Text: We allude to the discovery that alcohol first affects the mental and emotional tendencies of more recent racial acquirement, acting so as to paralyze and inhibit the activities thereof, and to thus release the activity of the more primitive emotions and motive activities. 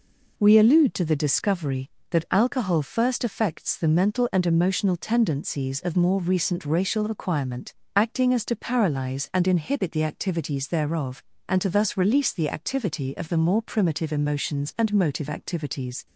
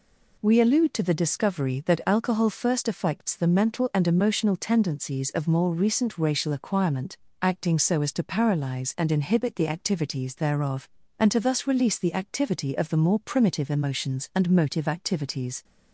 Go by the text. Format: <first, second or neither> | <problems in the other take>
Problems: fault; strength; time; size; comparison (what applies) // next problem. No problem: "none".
second | skips "so"; at 8.3 s